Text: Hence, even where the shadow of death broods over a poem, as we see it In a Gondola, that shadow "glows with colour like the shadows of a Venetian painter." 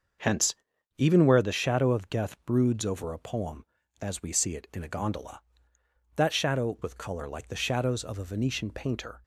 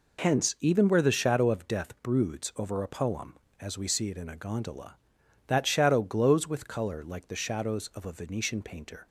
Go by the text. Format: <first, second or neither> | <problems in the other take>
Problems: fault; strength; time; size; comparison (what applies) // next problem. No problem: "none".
second | starts louder than the rest; until 1.6 s; 6.5 dB // skips "glows"; at 6.7 s